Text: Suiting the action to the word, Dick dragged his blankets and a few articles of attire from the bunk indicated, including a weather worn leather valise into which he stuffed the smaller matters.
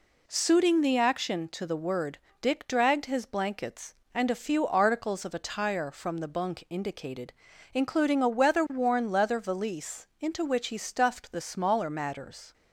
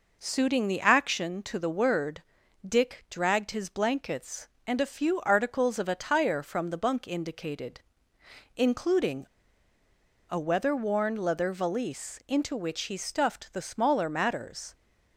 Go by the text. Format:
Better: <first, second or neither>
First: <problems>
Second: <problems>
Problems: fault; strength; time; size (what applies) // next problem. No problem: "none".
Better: first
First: none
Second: pauses between "including" and "a"; at 9.2 s; 1.0 s long